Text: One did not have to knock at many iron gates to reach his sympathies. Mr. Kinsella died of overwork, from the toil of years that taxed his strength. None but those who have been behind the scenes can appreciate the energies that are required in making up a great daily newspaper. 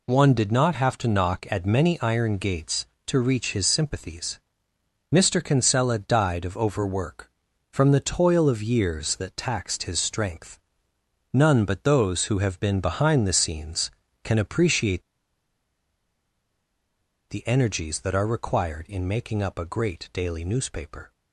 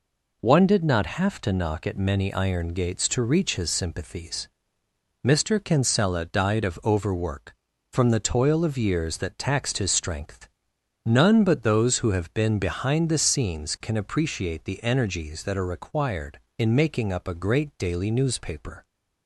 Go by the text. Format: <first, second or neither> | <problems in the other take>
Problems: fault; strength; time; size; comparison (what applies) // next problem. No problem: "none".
second | pauses between "appreciate" and "the"; strong; at 15.0 s; 2.2 s long